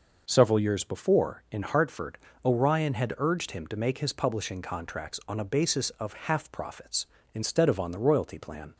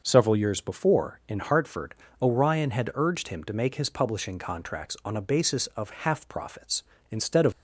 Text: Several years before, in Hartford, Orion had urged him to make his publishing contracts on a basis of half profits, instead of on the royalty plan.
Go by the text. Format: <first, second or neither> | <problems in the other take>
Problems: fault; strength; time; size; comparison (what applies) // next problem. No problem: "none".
first | stops before "on the royalty plan"; at 7.5 s